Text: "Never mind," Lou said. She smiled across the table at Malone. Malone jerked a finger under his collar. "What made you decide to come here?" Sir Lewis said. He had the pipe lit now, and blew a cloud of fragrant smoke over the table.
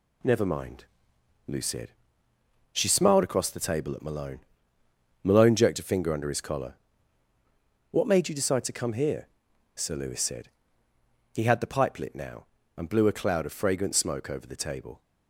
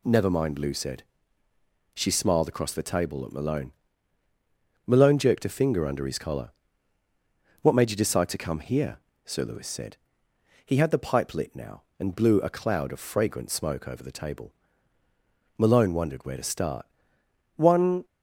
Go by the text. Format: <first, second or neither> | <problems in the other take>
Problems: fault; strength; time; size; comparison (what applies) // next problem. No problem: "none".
first | goes on to say "Malone wondered where to start One"; strong; from 15.5 s on; 2.4 s long